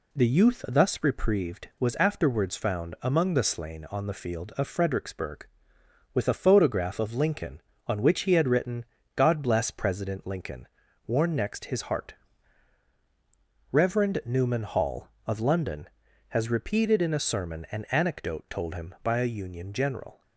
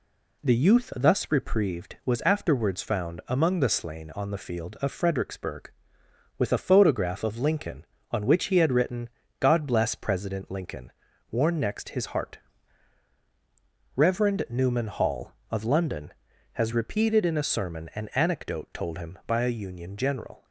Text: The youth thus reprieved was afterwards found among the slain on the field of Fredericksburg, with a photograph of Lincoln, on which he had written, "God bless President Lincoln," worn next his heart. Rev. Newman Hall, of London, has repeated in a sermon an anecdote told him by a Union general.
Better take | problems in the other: neither | none

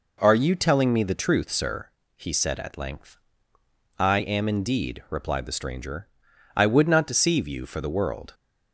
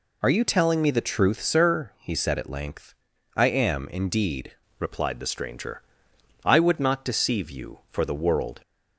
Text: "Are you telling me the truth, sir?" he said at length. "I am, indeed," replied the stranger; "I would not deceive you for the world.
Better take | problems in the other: first | changes voice at "replied"; from 4.7 s on; 3.9 s long

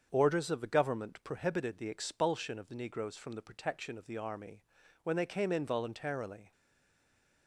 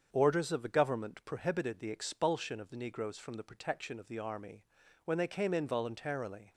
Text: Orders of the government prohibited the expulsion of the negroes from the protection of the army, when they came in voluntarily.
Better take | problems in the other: second | starts louder than the rest; strong; until 1.1 s; 7 dB; strong in the second // stays silent after the last word; from 6.5 s on; 0.9 s long

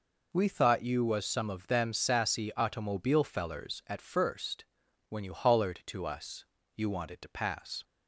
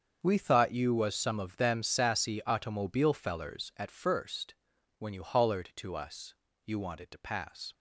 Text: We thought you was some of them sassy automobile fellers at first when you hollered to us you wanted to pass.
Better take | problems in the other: first | gets quieter; strong; throughout; 13 dB // pauses between "first" and "when"; noticeable; at 4.5 s; 0.46 s long; noticeable in the first // pauses between "us" and "you"; slight; at 6.3 s; 0.32 s long; slight in the first

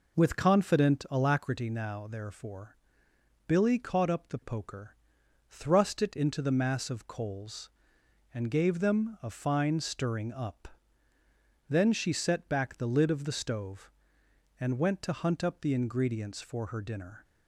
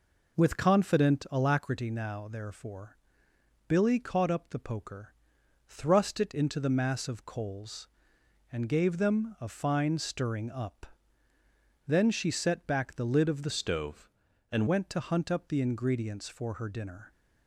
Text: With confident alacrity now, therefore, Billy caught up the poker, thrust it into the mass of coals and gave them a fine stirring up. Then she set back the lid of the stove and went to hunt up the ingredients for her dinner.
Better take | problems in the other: first | changes voice from "stove" to "and"; from 13.5 to 14.6 s; 1.1 s long

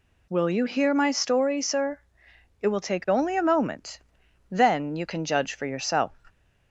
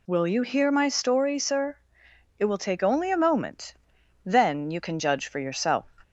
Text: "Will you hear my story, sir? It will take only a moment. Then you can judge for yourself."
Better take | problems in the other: neither | none

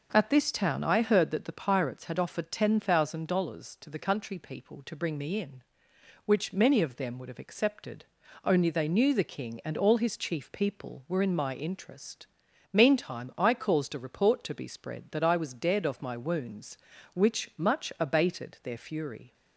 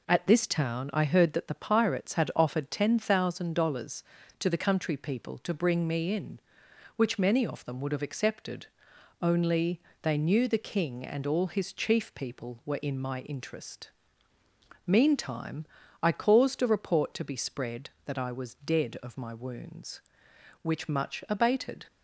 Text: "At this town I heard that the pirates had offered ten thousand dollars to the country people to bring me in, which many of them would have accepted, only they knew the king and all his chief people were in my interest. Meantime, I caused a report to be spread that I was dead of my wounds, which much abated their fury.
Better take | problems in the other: first | pauses between "only" and "they"; slight; at 9.8 s; 0.22 s long // stops before "their fury"; at 21.8 s

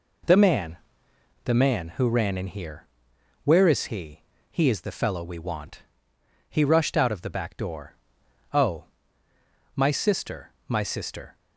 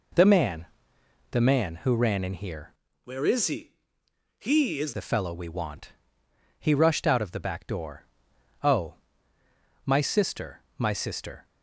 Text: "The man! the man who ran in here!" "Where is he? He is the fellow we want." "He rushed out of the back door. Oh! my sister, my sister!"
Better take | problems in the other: first | changes voice from "Where" to "is"; from 3.0 to 4.9 s; 1.9 s long

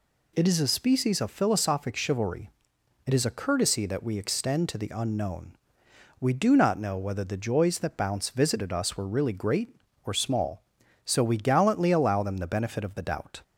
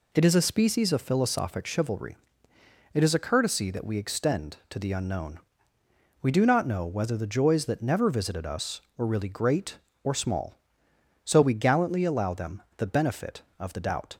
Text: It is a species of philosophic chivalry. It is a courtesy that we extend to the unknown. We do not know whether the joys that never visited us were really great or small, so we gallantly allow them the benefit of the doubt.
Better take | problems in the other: second | says "bounce" for "never"; at 7.9 s

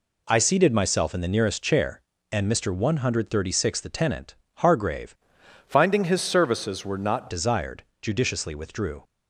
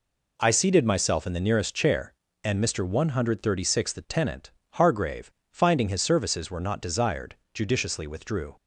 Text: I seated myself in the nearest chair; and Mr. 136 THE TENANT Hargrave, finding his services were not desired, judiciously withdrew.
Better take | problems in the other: second | pauses between "TENANT" and "Hargrave"; slight; at 4.3 s; 0.24 s long; slight in the second // changes voice from "finding" to "not"; from 5.6 to 7.3 s; 1.7 s long

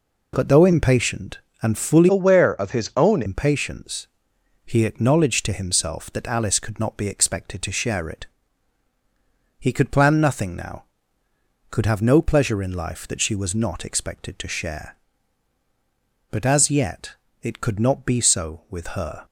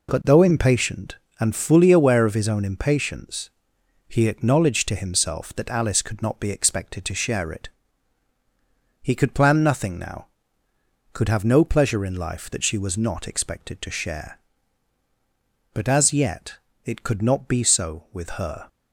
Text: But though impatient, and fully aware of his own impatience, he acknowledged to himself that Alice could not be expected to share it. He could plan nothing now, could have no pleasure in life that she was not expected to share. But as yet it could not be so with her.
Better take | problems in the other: second | changes voice from "aware" to "own"; from 2.0 to 3.2 s; 1.2 s long // pauses between "yet" and "it"; slight; at 17.1 s; 0.26 s long; slight in the second

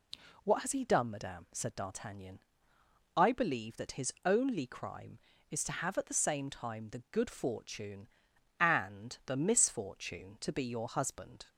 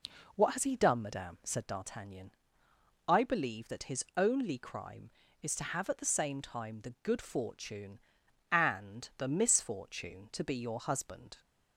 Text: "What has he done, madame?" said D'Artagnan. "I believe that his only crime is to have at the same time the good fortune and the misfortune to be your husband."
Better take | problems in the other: first | starts louder than the rest; noticeable; until 1.8 s; 4 dB

